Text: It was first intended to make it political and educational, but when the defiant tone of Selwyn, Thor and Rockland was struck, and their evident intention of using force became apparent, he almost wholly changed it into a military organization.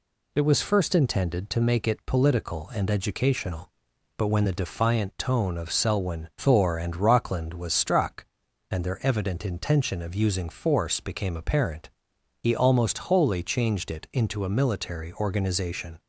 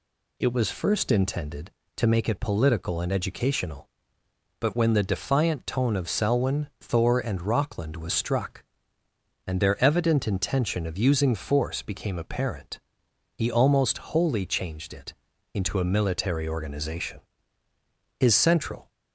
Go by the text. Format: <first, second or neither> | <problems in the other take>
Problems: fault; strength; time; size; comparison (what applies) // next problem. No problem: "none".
first | pauses between "it" and "into"; at 15.1 s; 0.38 s long // goes on to say "His central"; noticeable; from 18.1 s on; 0.70 s long